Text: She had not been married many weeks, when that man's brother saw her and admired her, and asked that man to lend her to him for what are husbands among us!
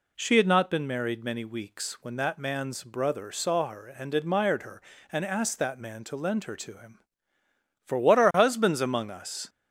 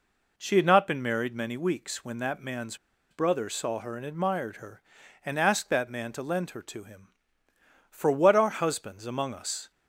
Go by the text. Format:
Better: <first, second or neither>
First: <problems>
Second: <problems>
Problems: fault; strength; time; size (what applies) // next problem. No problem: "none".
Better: first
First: none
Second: pauses between "man's" and "brother"; slight; at 2.7 s; 0.34 s long